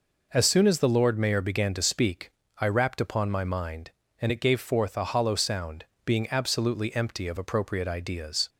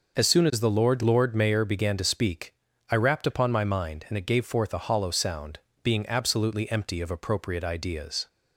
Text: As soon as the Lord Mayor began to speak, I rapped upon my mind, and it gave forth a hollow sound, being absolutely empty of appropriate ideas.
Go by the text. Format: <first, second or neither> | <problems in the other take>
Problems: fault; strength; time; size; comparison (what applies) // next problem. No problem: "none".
first | says "Lord" twice; at 1.0 s